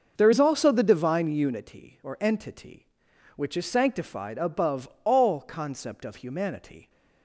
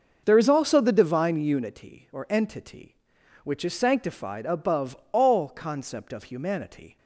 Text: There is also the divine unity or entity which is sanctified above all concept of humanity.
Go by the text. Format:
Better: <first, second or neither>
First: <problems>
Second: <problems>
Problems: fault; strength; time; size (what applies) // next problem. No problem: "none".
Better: neither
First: starts louder than the rest; noticeable; until 1.1 s; 6 dB // pauses between "above" and "all"; slight; at 4.8 s; 0.16 s long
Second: starts louder than the rest; noticeable; until 1.2 s; 6 dB // pauses between "above" and "all"; slight; at 4.9 s; 0.16 s long